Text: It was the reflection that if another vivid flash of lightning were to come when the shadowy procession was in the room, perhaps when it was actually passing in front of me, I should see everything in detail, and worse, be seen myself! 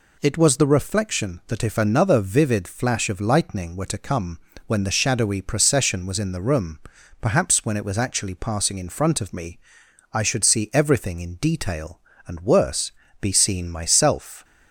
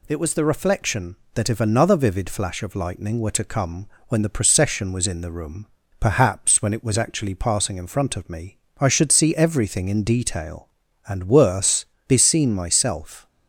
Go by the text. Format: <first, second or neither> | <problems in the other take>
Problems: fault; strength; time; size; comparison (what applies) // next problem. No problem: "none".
first | pauses between "come" and "when"; slight; at 3.8 s; 0.22 s long; slight in the first // skips "shadowy"; at 4.2 s